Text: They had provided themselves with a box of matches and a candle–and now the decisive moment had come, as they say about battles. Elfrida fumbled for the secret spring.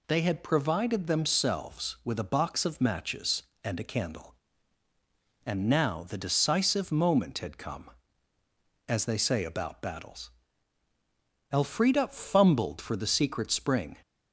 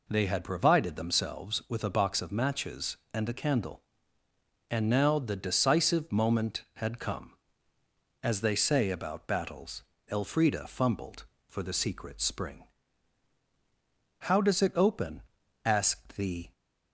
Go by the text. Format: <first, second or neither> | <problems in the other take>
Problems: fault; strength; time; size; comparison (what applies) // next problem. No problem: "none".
first | goes on to say "How does it open asked the"; strong; from 14.1 s on; 2.3 s long